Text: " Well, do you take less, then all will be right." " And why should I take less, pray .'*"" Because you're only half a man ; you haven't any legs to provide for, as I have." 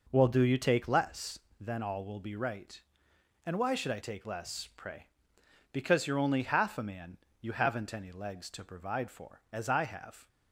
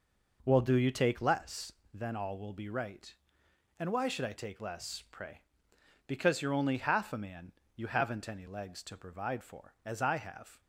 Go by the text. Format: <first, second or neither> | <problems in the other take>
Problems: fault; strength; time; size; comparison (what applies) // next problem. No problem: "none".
neither | none